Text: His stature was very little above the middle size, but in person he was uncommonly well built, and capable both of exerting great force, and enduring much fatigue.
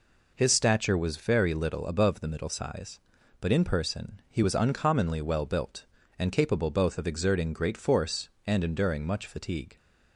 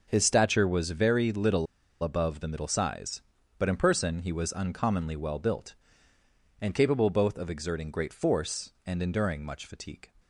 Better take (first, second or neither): first